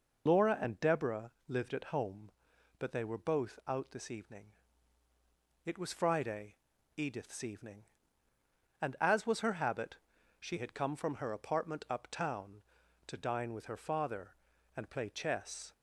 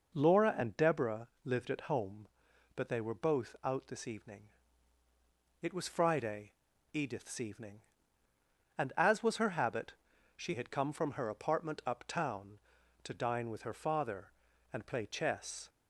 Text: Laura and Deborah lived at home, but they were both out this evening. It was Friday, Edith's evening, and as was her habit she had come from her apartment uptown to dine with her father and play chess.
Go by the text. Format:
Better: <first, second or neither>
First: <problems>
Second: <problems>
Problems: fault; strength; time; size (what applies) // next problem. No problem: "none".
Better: second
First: loses the start of "Laura"; at 0.2 s; 80 ms // pauses between "Deborah" and "lived"; slight; at 1.2 s; 0.16 s long // pauses between "habit" and "she"; at 9.9 s; 0.42 s long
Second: pauses between "Deborah" and "lived"; slight; at 1.2 s; 0.16 s long // pauses between "habit" and "she"; at 9.9 s; 0.42 s long